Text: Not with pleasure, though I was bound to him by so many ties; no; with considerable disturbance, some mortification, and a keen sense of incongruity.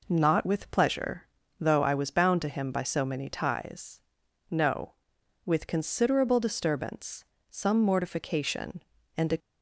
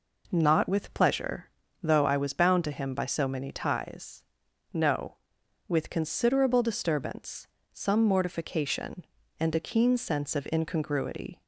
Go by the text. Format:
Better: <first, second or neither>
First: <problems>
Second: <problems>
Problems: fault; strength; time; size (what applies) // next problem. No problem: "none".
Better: second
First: stops before "keen sense of incongruity"; at 9.3 s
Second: none